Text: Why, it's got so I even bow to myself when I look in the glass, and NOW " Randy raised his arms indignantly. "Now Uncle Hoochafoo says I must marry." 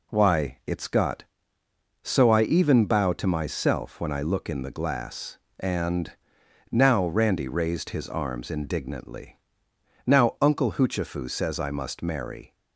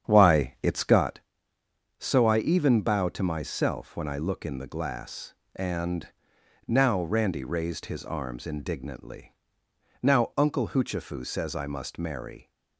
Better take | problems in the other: first | starts louder than the rest; strong; until 1.1 s; 8.5 dB // pauses between "and" and "NOW"; noticeable; at 6.0 s; 0.60 s long; noticeable in the first

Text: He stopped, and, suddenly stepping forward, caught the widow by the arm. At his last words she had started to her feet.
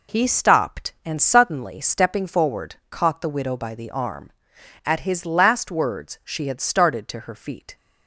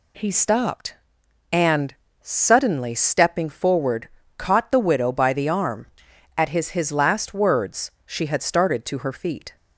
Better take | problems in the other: first | says "his" twice; at 6.6 s // pauses between "words" and "she"; slight; at 7.8 s; 0.16 s long

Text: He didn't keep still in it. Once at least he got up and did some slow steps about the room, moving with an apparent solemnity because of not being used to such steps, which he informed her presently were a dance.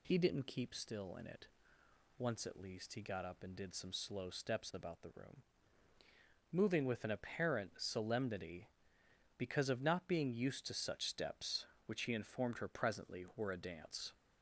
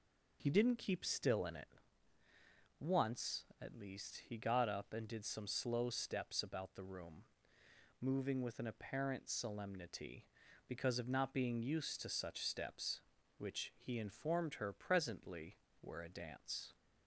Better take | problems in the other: neither | none

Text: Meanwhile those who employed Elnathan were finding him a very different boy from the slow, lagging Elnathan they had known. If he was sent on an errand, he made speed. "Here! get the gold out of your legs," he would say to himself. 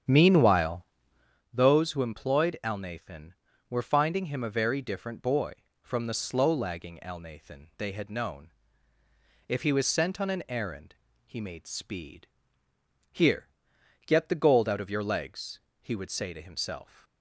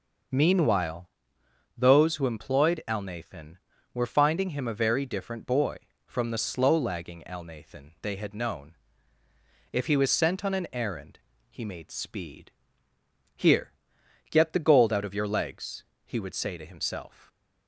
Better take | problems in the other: second | starts louder than the rest; strong; until 1.4 s; 8.5 dB // pauses between "Meanwhile" and "those"; noticeable; at 0.8 s; 0.68 s long; noticeable in the second

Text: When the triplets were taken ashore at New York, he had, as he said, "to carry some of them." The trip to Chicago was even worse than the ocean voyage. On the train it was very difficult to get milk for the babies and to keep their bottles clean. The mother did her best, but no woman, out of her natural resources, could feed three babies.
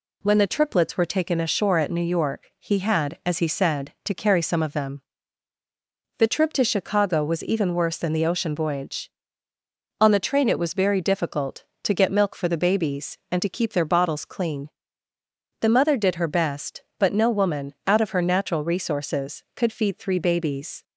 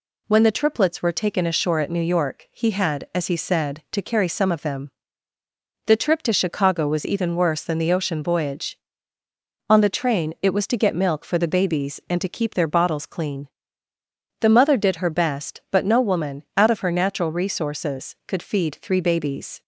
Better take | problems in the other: first | skips "very difficult"; at 10.6 s

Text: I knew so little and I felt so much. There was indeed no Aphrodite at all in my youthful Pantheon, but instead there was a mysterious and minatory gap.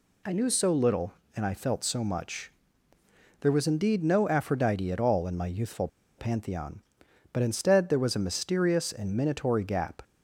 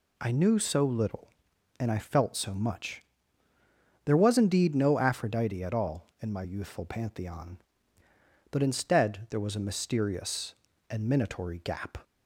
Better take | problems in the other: second | pauses between "youthful" and "Pantheon"; slight; at 5.8 s; 0.30 s long

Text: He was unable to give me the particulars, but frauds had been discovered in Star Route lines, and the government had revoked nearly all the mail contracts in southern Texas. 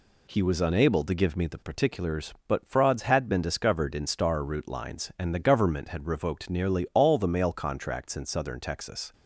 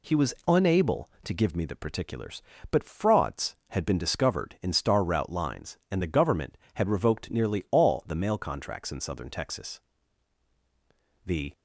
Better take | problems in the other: first | goes on to say "The"; slight; from 11.2 s on; 0.30 s long

